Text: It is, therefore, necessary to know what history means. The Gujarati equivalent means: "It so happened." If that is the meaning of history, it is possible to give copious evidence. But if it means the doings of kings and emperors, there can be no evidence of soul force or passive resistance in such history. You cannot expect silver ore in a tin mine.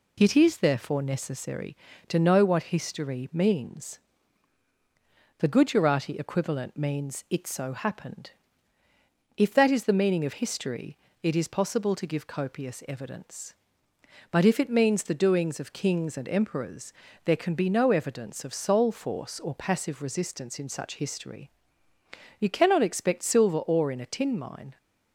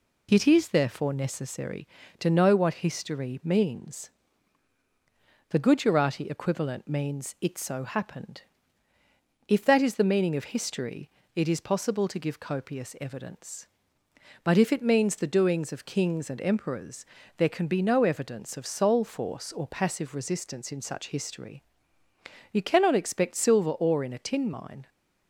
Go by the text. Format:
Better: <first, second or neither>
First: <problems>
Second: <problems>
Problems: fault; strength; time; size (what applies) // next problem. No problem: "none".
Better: neither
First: none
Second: none